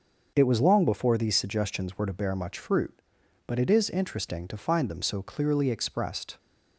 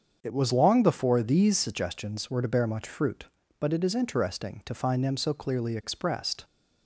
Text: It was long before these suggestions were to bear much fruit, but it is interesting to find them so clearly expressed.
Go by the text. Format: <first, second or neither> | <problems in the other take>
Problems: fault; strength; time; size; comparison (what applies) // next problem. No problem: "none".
neither | starts louder than the rest; the same in both